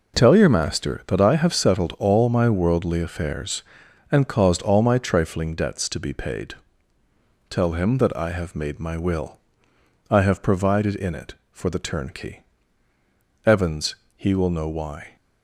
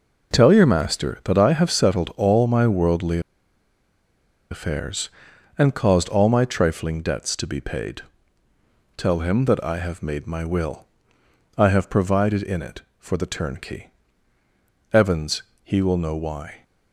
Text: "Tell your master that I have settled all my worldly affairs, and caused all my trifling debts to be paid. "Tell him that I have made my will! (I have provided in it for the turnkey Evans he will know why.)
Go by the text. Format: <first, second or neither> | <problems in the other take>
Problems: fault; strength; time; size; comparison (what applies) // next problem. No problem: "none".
first | pauses between "worldly" and "affairs"; strong; at 3.1 s; 1.3 s long // pauses between "turnkey" and "Evans"; at 13.9 s; 1.0 s long; also in the first // pauses between "Evans" and "he"; slight; at 15.4 s; 0.20 s long; slight in the first